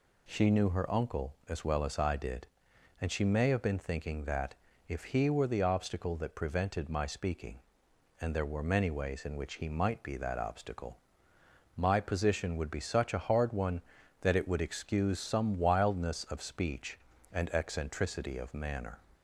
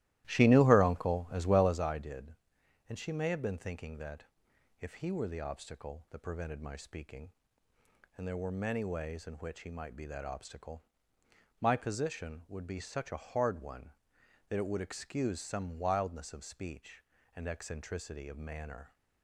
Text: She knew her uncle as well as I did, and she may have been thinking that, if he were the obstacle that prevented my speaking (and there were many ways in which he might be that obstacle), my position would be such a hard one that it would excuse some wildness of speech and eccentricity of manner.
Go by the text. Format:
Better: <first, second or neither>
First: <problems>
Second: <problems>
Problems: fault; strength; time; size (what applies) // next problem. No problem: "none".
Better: first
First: none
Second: starts louder than the rest; strong; until 1.8 s; 15.5 dB